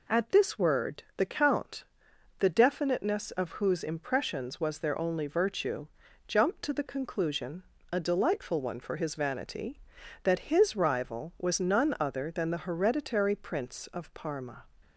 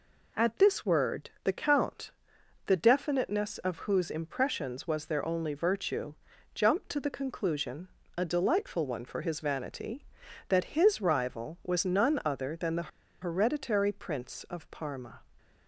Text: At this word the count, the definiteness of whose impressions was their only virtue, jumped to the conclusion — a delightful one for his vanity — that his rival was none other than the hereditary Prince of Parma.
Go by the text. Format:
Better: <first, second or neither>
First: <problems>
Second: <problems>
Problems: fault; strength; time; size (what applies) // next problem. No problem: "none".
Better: first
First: none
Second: pauses between "the" and "hereditary"; slight; at 12.8 s; 0.31 s long